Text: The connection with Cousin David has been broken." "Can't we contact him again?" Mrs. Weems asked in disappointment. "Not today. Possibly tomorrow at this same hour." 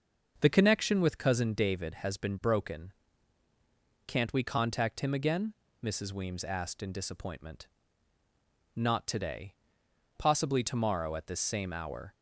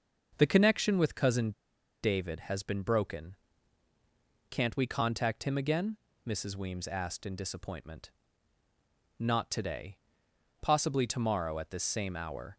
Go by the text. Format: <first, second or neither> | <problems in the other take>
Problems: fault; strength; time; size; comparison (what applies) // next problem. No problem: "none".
first | starts louder than the rest; until 1.3 s; 6.5 dB; also in the first // pauses between "Cousin" and "David"; noticeable; at 1.5 s; 0.51 s long